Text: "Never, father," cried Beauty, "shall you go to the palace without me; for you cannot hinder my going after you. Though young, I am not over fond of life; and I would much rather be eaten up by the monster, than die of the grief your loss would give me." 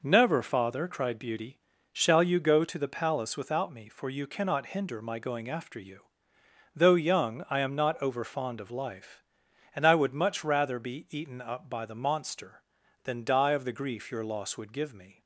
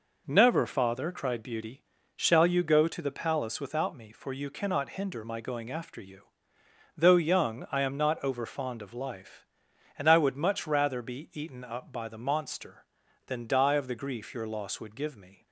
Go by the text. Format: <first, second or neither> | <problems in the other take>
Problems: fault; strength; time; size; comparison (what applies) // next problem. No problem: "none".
neither | none